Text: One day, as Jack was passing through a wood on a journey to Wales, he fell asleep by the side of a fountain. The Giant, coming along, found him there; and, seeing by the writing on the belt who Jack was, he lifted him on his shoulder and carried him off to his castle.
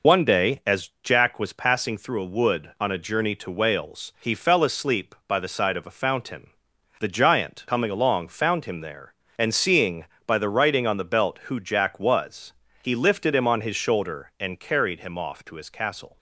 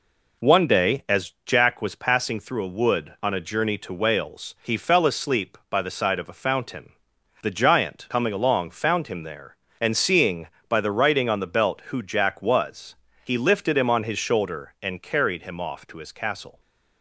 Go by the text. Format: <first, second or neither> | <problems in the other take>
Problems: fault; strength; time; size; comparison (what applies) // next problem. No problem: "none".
second | loses the start of "One"; at 0.0 s; 75 ms